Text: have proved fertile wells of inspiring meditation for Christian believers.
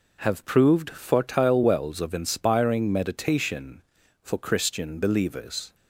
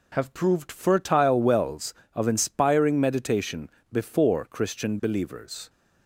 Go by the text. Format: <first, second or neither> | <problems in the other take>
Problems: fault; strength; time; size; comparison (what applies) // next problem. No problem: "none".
first | says "before" for "for"; at 3.9 s